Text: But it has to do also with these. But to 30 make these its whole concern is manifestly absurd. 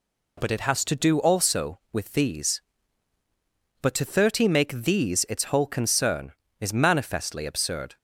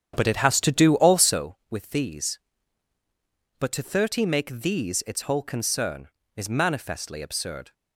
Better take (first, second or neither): first